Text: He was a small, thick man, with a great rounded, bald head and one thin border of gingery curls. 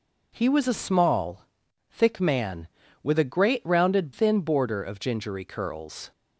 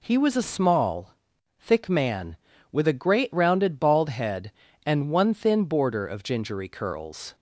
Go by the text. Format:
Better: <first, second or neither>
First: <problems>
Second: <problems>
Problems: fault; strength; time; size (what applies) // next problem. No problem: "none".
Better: second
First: skips "bald head and one"; at 4.1 s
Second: none